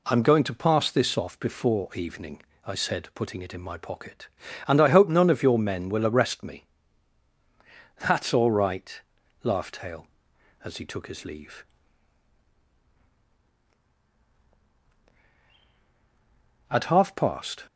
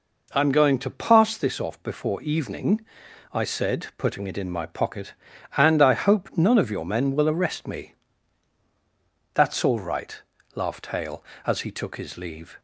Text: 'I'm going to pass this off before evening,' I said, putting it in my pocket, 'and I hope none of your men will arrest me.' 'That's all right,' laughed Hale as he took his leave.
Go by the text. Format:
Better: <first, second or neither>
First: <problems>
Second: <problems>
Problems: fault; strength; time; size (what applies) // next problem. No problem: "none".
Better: second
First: goes on to say "At half past"; noticeable; from 16.6 s on; 0.94 s long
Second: none